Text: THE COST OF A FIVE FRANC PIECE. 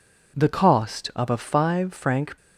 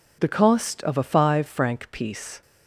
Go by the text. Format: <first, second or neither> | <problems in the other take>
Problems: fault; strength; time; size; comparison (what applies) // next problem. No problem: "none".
second | stops before "PIECE"; at 2.3 s